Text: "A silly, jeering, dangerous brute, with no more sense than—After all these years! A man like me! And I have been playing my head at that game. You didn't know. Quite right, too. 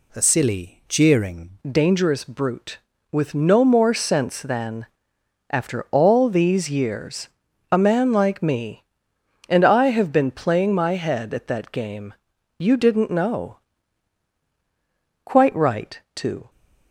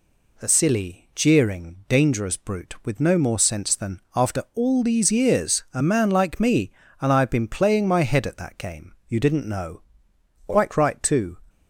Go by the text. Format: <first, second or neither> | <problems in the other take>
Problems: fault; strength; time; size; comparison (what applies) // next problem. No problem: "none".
second | changes voice at "dangerous"; from 1.6 s on; 14.8 s long